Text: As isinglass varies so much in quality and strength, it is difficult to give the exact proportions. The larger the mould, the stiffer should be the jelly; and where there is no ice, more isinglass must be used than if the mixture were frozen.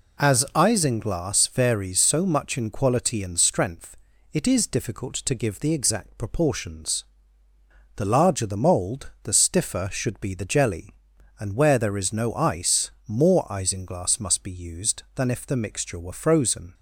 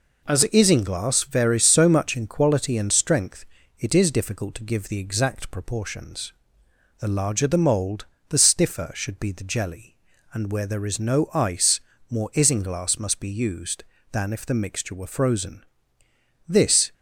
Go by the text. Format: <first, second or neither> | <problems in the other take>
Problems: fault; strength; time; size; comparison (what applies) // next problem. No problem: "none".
first | goes on to say "This"; slight; from 16.4 s on; 0.46 s long